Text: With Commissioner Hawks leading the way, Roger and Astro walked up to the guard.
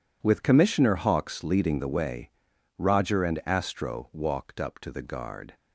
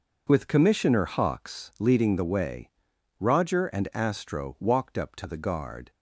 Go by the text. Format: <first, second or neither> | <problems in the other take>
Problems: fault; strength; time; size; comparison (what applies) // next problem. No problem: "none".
neither | none